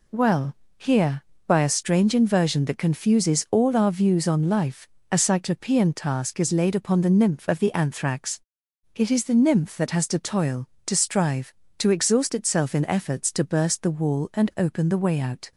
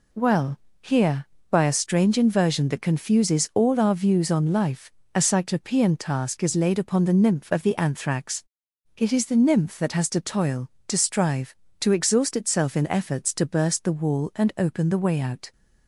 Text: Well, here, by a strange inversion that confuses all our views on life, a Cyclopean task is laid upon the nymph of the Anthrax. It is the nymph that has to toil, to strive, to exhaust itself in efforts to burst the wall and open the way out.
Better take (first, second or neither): neither